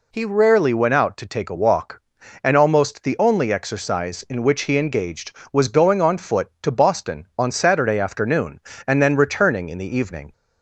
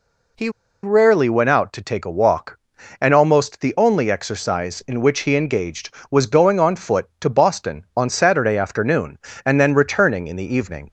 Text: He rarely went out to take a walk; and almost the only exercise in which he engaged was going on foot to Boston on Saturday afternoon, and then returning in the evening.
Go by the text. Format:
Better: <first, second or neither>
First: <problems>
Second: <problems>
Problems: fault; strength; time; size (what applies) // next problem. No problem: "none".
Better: first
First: none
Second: pauses between "He" and "rarely"; slight; at 0.4 s; 0.34 s long